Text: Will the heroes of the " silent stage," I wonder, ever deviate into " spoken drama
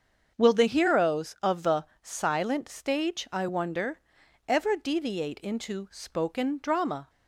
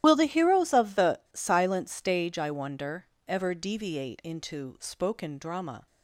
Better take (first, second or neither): first